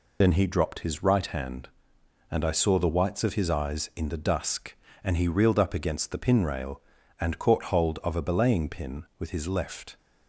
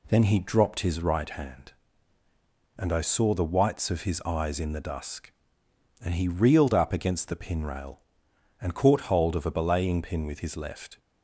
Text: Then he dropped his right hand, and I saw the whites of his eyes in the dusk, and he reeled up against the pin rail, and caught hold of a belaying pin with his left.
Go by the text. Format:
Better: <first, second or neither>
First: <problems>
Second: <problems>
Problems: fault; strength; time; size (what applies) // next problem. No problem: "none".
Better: second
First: loses the start of "Then"; at 0.2 s; 45 ms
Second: none